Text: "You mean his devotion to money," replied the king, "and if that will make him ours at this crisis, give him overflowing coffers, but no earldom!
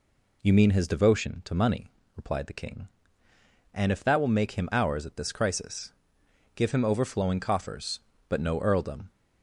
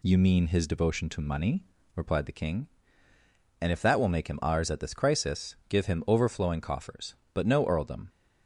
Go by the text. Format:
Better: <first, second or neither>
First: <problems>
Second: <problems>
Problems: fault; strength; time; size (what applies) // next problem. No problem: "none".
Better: neither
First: none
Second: none